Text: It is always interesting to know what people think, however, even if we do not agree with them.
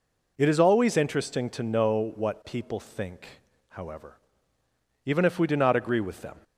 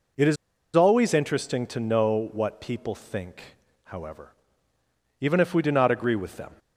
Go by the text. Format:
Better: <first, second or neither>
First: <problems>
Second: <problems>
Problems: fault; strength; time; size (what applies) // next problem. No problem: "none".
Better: first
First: none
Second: pauses between "is" and "always"; at 0.3 s; 0.40 s long